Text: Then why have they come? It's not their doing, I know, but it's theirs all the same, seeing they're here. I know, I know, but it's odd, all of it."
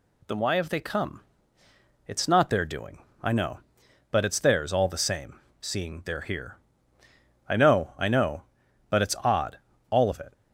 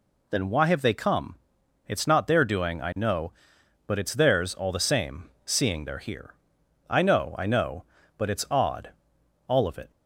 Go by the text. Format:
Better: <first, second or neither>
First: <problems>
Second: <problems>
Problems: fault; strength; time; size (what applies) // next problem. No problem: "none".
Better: neither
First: none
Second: none